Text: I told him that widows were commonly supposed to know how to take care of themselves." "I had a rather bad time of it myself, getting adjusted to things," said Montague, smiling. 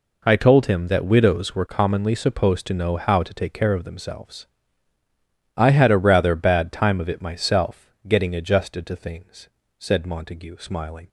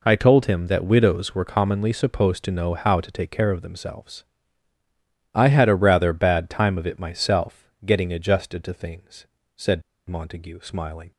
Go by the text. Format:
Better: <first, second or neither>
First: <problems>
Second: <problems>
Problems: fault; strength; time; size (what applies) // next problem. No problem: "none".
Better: first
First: none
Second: pauses between "said" and "Montague"; slight; at 9.8 s; 0.27 s long